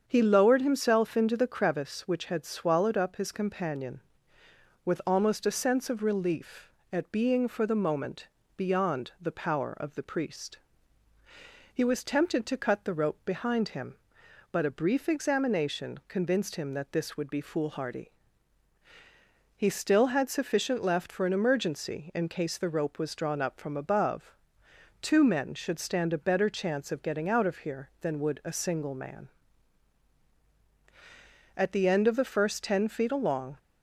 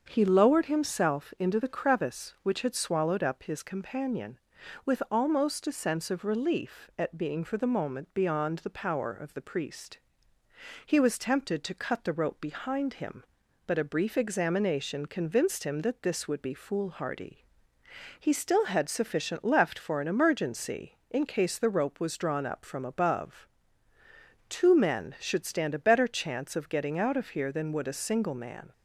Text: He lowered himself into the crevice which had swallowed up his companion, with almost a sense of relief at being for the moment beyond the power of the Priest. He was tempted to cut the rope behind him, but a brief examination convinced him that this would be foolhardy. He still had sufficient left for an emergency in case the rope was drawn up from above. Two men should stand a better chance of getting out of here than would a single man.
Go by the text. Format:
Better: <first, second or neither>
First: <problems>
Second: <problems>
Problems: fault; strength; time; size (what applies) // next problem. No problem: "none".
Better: second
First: starts louder than the rest; strong; until 1.0 s; 7.5 dB // pauses between "moment" and "beyond"; slight; at 8.2 s; 0.28 s long // goes on to say "At the end of the first ten feet along"; strong; from 31.5 s on; 2.0 s long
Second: starts louder than the rest; until 1.0 s; 7 dB